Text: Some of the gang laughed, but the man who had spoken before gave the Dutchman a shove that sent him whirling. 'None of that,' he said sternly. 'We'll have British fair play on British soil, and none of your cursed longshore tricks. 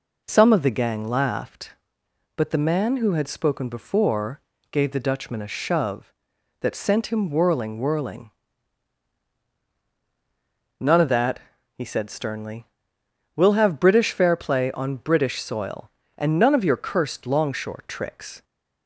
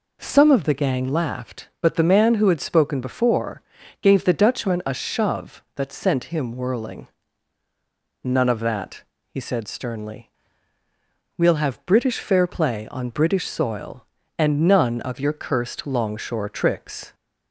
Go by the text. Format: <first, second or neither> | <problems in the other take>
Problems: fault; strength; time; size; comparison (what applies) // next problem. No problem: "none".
second | pauses between "before" and "gave"; slight; at 4.3 s; 0.32 s long; also in the second // says "whirling" twice; at 7.7 s